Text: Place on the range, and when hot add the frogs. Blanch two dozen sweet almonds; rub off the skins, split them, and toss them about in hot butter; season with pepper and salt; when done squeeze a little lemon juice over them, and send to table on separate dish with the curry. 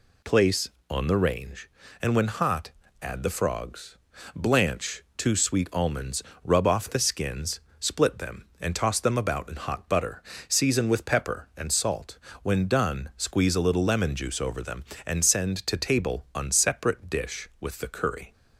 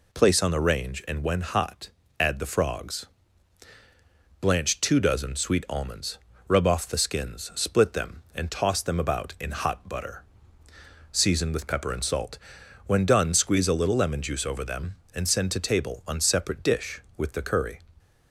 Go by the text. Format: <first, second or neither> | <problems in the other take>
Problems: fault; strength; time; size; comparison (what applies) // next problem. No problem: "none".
second | pauses between "hot" and "add"; slight; at 2.7 s; 0.30 s long; slight in the second // skips "dozen"; at 5.3 s